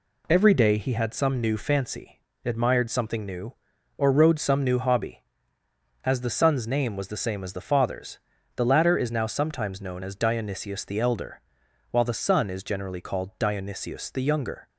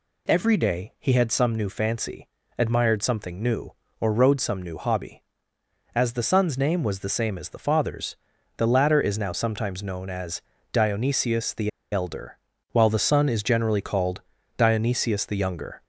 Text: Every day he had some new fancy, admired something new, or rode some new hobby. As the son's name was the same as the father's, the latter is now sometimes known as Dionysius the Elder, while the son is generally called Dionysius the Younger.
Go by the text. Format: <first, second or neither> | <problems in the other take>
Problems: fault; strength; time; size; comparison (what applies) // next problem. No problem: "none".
first | pauses between "as" and "Dionysius"; slight; at 10.4 s; 0.32 s long // pauses between "the" and "Elder"; slight; at 11.6 s; 0.23 s long // pauses between "called" and "Dionysius"; slight; at 14.2 s; 0.36 s long